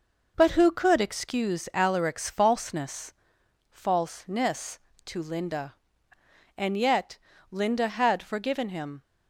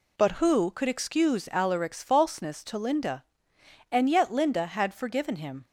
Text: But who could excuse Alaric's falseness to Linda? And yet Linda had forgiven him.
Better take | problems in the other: second | says "falseness" twice; at 3.6 s // pauses between "yet" and "Linda"; slight; at 7.1 s; 0.34 s long

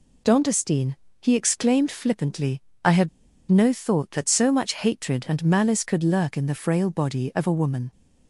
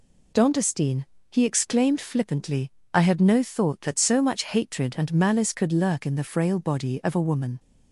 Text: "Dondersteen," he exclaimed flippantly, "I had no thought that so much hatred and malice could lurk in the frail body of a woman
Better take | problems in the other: second | pauses between "had" and "no"; at 3.0 s; 0.39 s long

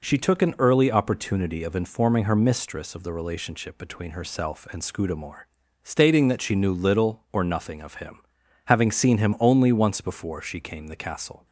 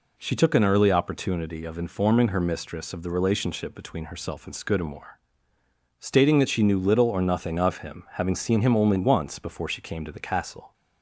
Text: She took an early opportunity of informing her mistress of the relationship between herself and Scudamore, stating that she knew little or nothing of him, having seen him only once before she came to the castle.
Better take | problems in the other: second | skips "to"; at 10.8 s

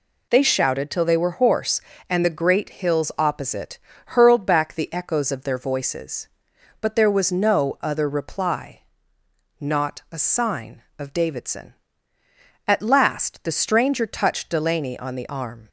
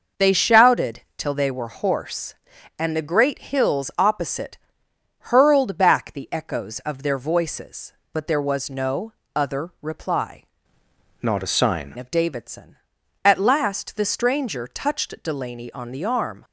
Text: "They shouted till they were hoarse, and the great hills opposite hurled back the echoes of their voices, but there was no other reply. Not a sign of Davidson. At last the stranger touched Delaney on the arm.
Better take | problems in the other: first | pauses between "shouted" and "till"; slight; at 1.0 s; 0.16 s long // pauses between "opposite" and "hurled"; noticeable; at 4.5 s; 0.70 s long; slight in the first // pauses between "no" and "other"; slight; at 9.1 s; 0.24 s long // changes voice from "Not" to "sign"; from 11.2 to 11.9 s; 0.7 s long

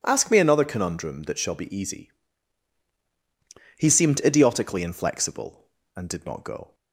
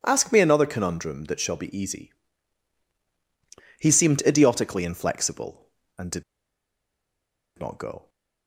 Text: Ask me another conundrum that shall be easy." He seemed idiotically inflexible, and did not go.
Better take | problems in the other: first | pauses between "did" and "not"; strong; at 6.2 s; 1.3 s long

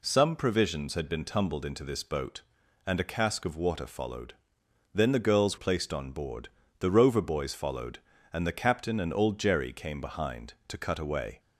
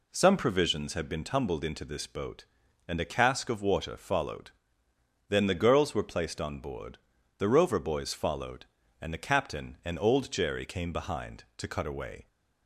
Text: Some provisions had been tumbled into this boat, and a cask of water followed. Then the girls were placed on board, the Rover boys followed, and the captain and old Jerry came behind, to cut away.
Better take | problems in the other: second | skips "were"; at 5.5 s

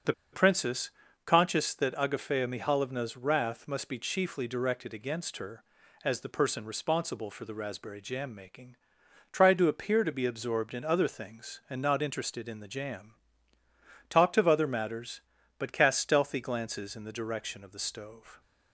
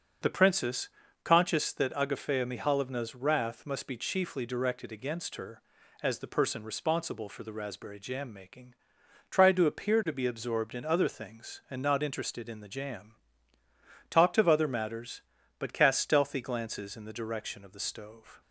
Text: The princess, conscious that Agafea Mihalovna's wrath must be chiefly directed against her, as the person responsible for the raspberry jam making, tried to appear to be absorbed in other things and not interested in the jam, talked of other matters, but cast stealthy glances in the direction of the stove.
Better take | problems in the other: second | starts louder than the rest; until 1.6 s; 6 dB; also in the second // pauses between "The" and "princess"; slight; at 0.1 s; 0.20 s long

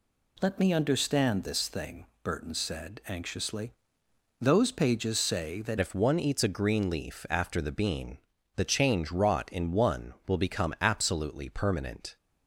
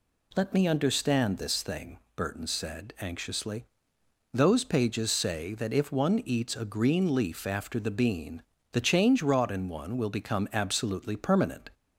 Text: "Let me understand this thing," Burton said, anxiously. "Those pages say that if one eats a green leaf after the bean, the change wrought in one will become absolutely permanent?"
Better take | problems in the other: second | changes voice at "if"; from 5.7 s on; 6.4 s long

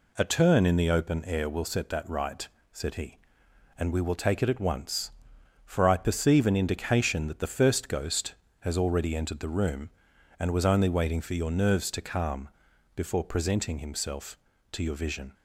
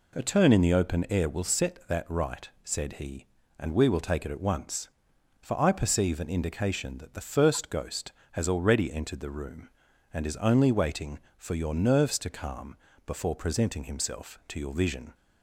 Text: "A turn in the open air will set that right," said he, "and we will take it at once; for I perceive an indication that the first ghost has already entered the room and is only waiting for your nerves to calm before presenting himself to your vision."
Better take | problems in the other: second | says "was" for "is"; at 10.5 s // pauses between "calm" and "before"; at 12.4 s; 0.44 s long; slight in the second

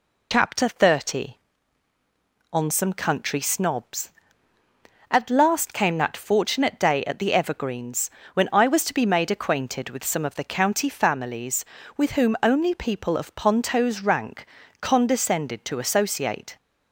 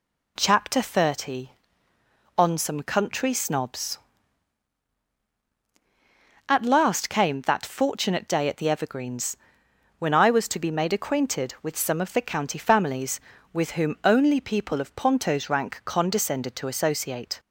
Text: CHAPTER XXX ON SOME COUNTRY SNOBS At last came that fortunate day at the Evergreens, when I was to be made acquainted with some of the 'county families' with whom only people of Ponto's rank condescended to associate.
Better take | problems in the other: second | loses the start of "CHAPTER"; at 0.3 s; 65 ms // pauses between "rank" and "condescended"; slight; at 14.4 s; 0.34 s long

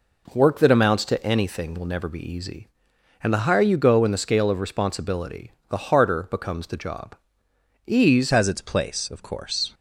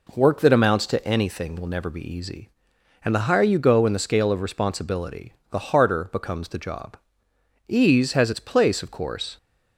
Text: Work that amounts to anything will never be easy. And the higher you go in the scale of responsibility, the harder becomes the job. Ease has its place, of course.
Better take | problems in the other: second | changes voice at "has"; from 8.3 s on; 1.4 s long

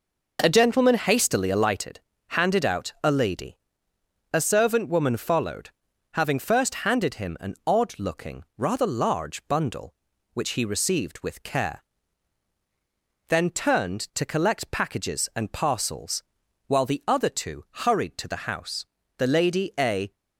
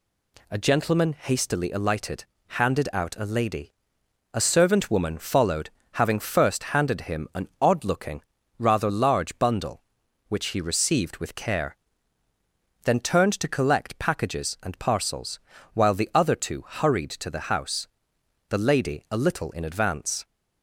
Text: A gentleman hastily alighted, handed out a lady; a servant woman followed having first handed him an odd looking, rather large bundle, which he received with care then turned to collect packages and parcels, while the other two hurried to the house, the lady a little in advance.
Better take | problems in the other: second | pauses between "followed" and "having"; at 5.6 s; 0.44 s long; slight in the second // pauses between "care" and "then"; strong; at 11.8 s; 1.4 s long; also in the second // pauses between "two" and "hurried"; slight; at 17.6 s; 0.22 s long // stops before "little in advance"; at 20.1 s

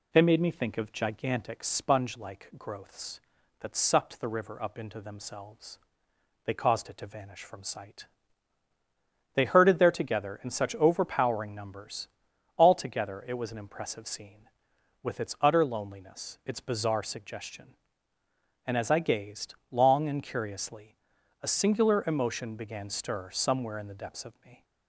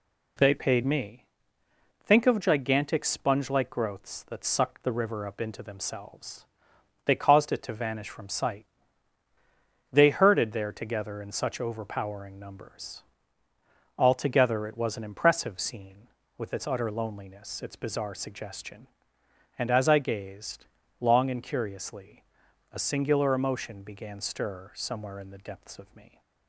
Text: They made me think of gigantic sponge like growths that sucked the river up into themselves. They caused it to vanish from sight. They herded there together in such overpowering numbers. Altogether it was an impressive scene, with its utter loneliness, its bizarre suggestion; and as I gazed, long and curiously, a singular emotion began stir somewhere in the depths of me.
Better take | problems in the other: first | says "paid" for "made"; at 0.5 s // pauses between "me" and "think"; noticeable; at 1.2 s; 0.80 s long

